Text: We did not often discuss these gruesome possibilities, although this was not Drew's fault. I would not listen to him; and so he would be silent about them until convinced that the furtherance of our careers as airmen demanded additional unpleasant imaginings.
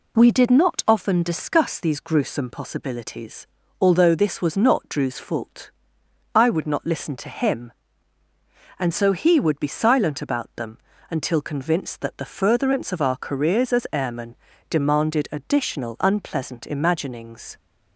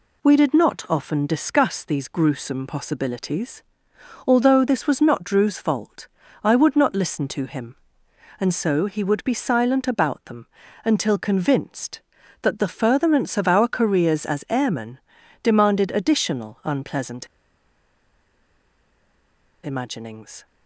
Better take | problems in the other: first | pauses between "them" and "until"; at 10.4 s; 0.38 s long; slight in the first // pauses between "airmen" and "demanded"; at 14.9 s; 0.42 s long; slight in the first // pauses between "unpleasant" and "imaginings"; strong; at 17.2 s; 2.3 s long

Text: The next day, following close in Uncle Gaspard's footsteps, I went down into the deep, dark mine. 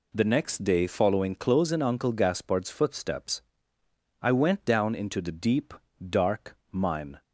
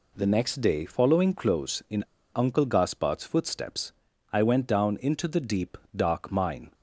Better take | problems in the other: first | pauses between "in" and "Uncle"; slight; at 2.0 s; 0.32 s long

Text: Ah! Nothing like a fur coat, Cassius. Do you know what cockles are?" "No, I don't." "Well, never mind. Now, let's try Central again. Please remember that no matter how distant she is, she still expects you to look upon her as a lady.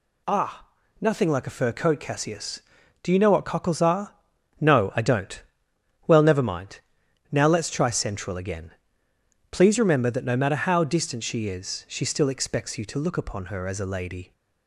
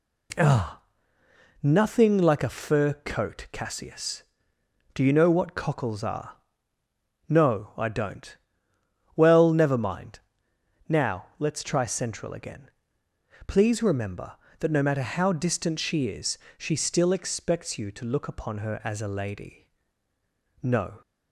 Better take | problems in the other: first | goes on to say "No"; slight; from 20.6 s on; 0.38 s long

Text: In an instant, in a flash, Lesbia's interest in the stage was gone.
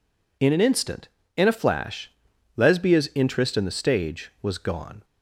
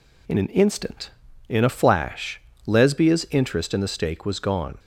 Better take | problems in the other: first | says "stake" for "stage"; at 3.8 s

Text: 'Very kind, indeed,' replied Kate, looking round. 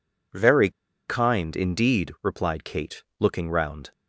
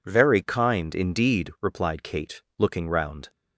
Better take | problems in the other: second | pauses between "Very" and "kind"; at 0.6 s; 0.37 s long

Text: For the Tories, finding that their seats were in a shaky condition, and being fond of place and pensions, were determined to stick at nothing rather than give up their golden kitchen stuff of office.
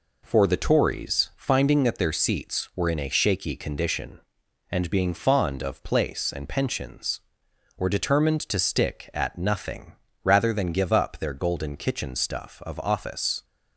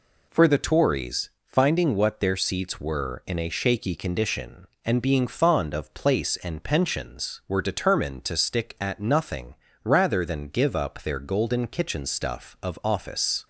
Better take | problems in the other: first | says "what" for "that"; at 1.9 s // pauses between "nothing" and "rather"; slight; at 9.5 s; 0.28 s long; slight in the first

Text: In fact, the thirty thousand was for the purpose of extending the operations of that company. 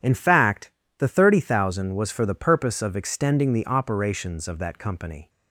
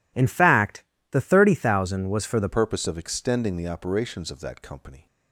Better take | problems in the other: first | changes voice at "purpose"; from 2.5 s on; 2.5 s long

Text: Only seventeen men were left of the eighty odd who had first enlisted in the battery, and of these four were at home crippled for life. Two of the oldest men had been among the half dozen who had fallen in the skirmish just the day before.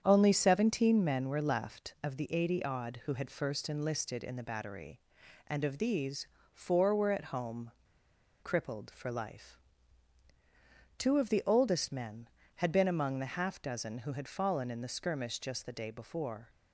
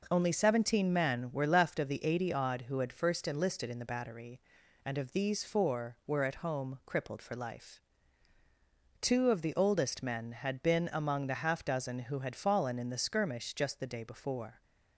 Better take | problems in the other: second | starts louder than the rest; strong; until 1.0 s; 8 dB // pauses between "these" and "four"; slight; at 6.2 s; 0.30 s long // pauses between "home" and "crippled"; noticeable; at 7.6 s; 0.72 s long

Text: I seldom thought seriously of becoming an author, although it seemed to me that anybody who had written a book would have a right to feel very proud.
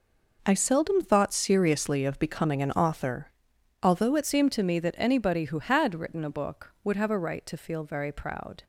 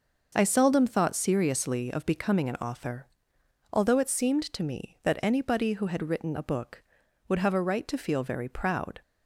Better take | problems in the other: second | changes voice at "seemed"; from 4.2 s on; 4.4 s long

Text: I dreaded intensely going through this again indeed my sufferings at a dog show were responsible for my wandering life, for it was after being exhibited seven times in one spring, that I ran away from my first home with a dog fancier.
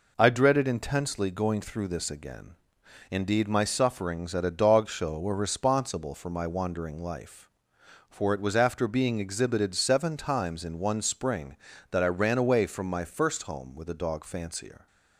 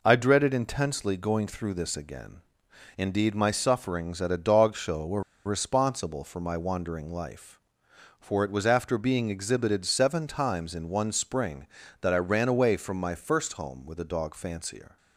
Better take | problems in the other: first | pauses between "again" and "indeed"; noticeable; at 2.4 s; 0.56 s long; noticeable in the first // pauses between "were" and "responsible"; slight; at 5.2 s; 0.25 s long

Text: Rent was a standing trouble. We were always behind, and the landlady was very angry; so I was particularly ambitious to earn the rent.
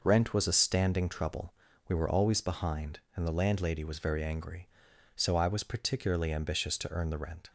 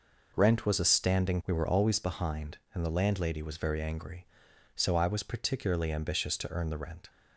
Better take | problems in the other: first | skips "trouble"; at 1.4 s

